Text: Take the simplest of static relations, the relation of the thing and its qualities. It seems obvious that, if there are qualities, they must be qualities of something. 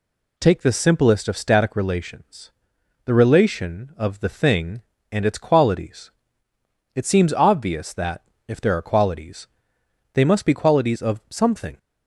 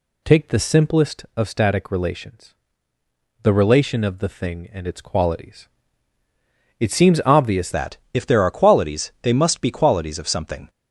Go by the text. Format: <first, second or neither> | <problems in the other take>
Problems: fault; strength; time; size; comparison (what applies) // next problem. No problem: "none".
first | changes voice at "that"; from 7.7 s on; 2.9 s long